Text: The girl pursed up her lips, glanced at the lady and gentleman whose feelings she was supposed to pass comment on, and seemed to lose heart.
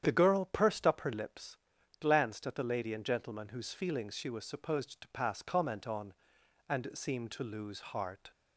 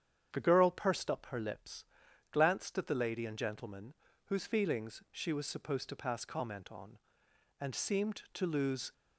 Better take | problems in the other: first | starts louder than the rest; strong; until 1.3 s; 8.5 dB; strong in the first // pauses between "gentleman" and "whose"; slight; at 3.9 s; 0.32 s long // stops before "heart"; at 8.9 s

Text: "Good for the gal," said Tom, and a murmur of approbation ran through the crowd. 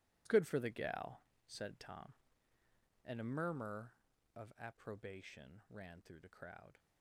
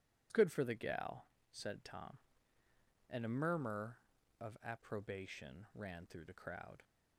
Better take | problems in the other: second | gets quieter; strong; throughout; 15.5 dB

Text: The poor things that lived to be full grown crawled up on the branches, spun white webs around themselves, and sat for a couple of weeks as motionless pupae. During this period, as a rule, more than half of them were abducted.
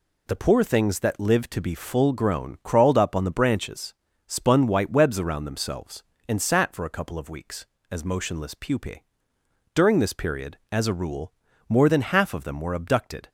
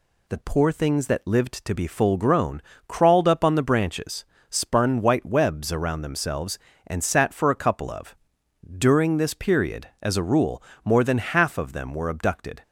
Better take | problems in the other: first | pauses between "grown" and "crawled"; slight; at 2.6 s; 0.26 s long // skips "weeks as motionless pupae"; at 8.4 s

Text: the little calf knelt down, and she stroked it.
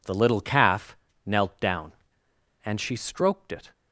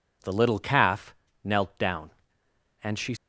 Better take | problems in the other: first | pauses between "calf" and "knelt"; slight; at 1.1 s; 0.28 s long; slight in the first // stops before "stroked it"; at 3.1 s

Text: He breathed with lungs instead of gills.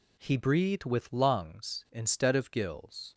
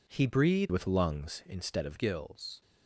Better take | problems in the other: first | changes voice from "with" to "of"; from 0.6 to 1.9 s; 1.3 s long

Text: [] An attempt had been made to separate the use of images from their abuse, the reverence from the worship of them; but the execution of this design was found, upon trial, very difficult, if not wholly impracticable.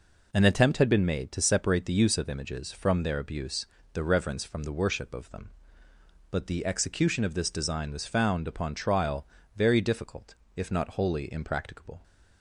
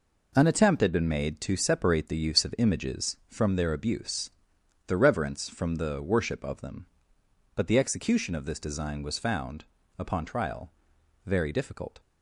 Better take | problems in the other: first | stops before "if not wholly impracticable"; at 11.9 s

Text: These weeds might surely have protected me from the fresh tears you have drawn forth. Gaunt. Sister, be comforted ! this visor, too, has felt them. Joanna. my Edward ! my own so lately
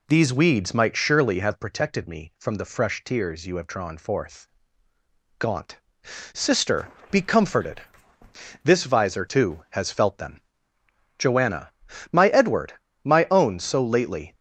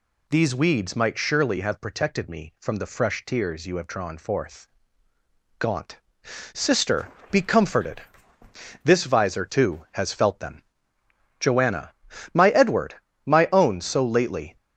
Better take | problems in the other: second | starts louder than the rest; slight; until 1.7 s; 2 dB

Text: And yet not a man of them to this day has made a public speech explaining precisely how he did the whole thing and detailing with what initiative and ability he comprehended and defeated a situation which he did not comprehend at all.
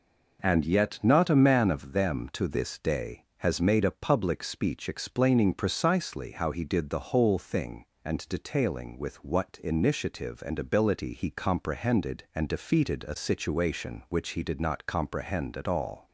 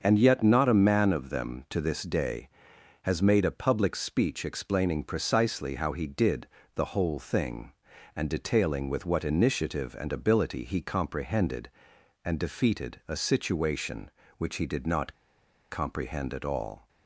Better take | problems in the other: first | starts louder than the rest; until 1.0 s; 6.5 dB // pauses between "did" and "the"; slight; at 6.4 s; 0.26 s long // pauses between "not" and "comprehend"; noticeable; at 15.1 s; 0.56 s long

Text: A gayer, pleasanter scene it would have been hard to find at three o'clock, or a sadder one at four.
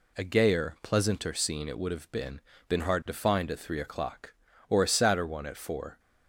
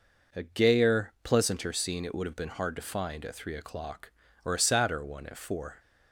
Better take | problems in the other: second | says "been" twice; at 2.6 s

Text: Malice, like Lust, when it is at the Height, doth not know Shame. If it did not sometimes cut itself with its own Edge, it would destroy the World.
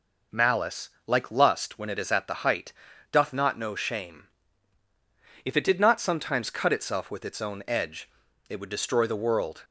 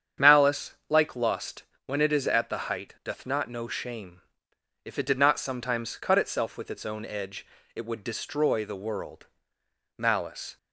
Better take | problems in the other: first | starts louder than the rest; strong; until 1.3 s; 8 dB // goes on to say "Malice"; from 9.9 s on; 0.60 s long

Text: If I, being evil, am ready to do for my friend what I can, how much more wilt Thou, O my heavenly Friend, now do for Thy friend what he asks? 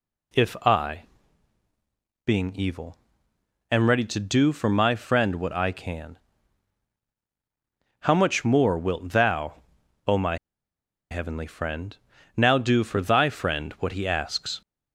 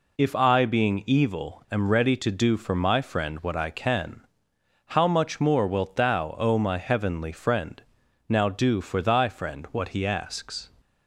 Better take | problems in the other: second | pauses between "my" and "heavenly"; noticeable; at 10.3 s; 0.73 s long

